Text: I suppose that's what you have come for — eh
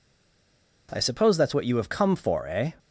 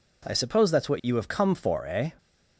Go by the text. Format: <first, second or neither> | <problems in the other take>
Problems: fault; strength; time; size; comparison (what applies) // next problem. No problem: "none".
second | stays silent before the first word; slight; until 0.8 s; 0.8 s long